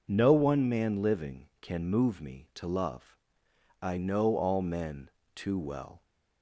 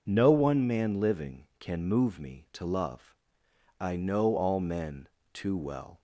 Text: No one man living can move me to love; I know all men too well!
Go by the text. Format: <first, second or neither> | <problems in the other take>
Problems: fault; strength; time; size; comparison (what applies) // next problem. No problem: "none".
neither | pauses between "men" and "too"; slight; the same in both